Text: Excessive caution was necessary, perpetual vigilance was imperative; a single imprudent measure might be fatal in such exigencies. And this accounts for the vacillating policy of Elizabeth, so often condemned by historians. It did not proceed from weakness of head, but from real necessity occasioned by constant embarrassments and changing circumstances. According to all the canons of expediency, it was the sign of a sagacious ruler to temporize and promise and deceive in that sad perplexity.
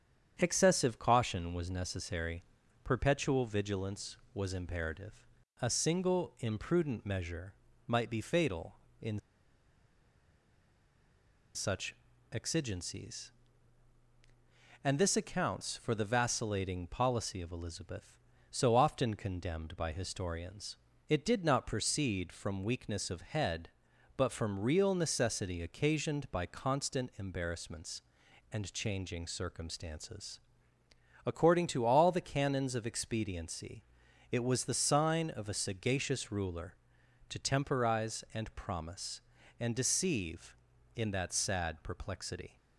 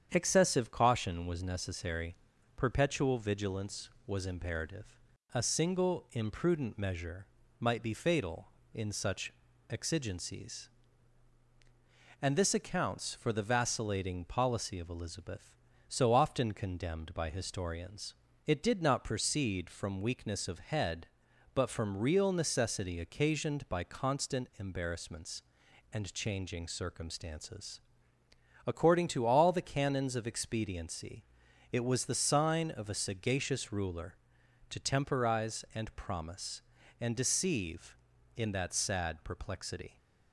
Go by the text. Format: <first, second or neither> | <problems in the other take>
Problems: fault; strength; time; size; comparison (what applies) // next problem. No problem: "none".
second | starts louder than the rest; strong; until 1.4 s; 8 dB; strong in the second // pauses between "measure" and "might"; slight; at 7.5 s; 0.34 s long; slight in the second // pauses between "in" and "such"; strong; at 9.1 s; 2.3 s long // pauses between "such" and "exigencies"; at 11.9 s; 0.38 s long; also in the second